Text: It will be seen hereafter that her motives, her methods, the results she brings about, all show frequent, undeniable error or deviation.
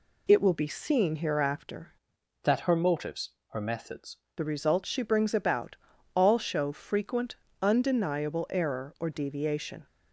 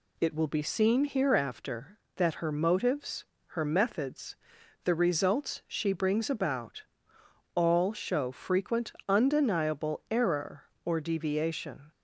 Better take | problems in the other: second | changes voice from "that" to "methods"; from 2.4 to 4.1 s; 1.7 s long

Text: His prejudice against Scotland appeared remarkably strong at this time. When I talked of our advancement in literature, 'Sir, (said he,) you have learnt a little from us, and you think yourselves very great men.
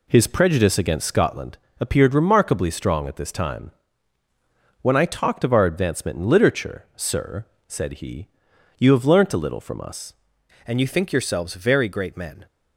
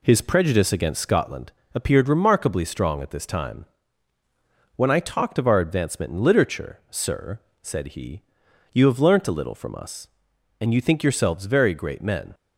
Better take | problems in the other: second | pauses between "Scotland" and "appeared"; slight; at 1.5 s; 0.20 s long; slight in the second // changes voice at "and"; from 10.6 s on; 1.8 s long

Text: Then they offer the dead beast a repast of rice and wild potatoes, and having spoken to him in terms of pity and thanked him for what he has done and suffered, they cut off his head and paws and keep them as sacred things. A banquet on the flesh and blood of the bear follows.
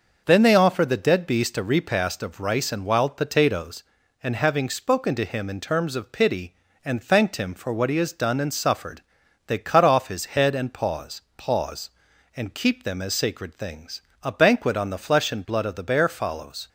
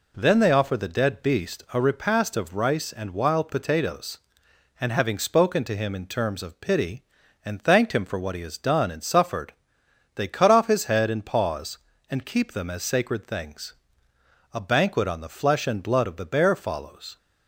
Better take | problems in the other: second | starts louder than the rest; noticeable; until 1.2 s; 6 dB // says "paws" twice; at 11.3 s

